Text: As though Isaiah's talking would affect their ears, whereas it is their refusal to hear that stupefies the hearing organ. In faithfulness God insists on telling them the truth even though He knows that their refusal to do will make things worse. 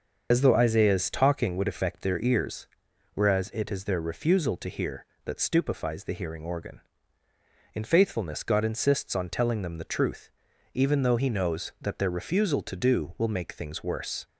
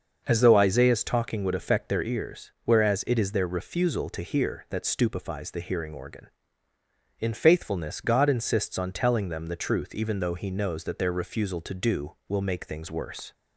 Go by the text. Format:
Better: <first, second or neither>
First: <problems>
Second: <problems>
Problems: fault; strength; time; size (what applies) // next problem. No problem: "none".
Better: second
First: loses the start of "As"; at 0.3 s; 90 ms // starts louder than the rest; until 1.3 s; 6.5 dB // pauses between "truth" and "even"; at 10.3 s; 0.44 s long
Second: starts louder than the rest; until 1.2 s; 6 dB